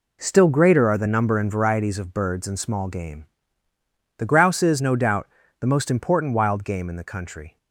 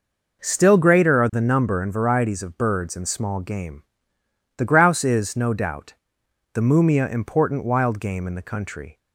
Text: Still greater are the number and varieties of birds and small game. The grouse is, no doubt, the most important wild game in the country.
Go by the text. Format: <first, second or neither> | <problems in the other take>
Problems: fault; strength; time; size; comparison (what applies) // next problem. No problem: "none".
first | says "mumia" for "most"; at 6.5 s